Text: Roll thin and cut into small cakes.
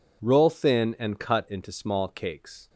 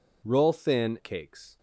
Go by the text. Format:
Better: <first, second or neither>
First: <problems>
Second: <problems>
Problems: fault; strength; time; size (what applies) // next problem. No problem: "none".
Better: first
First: none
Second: skips "and cut into small"; at 0.9 s